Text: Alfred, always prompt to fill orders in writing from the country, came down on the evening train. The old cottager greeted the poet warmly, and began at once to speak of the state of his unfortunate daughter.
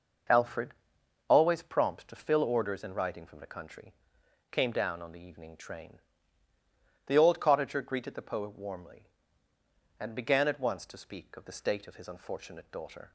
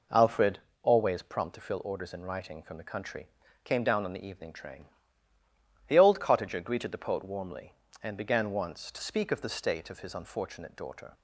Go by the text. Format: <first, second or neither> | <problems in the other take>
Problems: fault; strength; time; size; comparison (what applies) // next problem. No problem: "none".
first | skips "at"; at 8.5 s